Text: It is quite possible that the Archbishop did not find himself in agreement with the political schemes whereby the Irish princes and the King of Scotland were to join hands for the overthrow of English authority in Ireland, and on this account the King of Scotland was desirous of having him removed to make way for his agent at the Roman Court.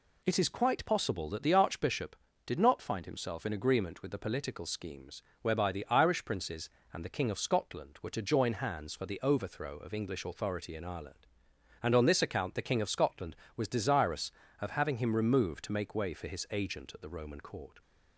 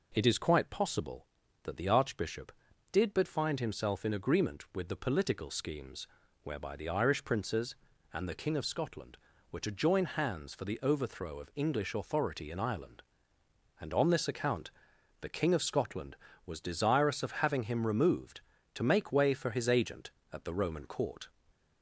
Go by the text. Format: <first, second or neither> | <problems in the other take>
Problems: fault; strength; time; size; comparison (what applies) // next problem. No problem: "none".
first | says "but" for "not"; at 3.1 s // pauses between "schemes" and "whereby"; slight; at 6.0 s; 0.36 s long; slight in the first // pauses between "account" and "the"; noticeable; at 14.6 s; 0.52 s long